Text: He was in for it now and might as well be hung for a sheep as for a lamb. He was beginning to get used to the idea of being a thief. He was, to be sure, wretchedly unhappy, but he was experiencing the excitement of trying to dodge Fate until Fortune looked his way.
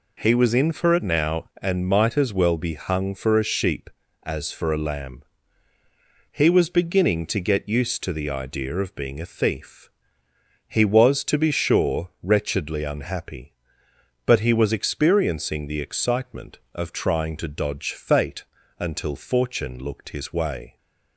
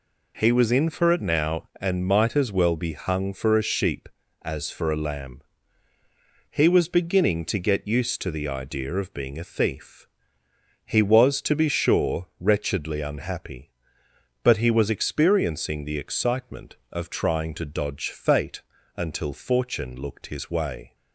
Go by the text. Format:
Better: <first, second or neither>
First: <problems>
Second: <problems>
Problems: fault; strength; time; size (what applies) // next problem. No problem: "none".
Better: neither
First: pauses between "Fate" and "until"; slight; at 18.4 s; 0.36 s long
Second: pauses between "Fate" and "until"; slight; at 18.6 s; 0.36 s long